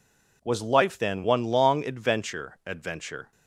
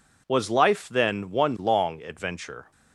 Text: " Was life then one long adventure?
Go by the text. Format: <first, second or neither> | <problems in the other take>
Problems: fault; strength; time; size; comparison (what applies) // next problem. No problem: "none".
second | says "adventure" twice; at 2.6 s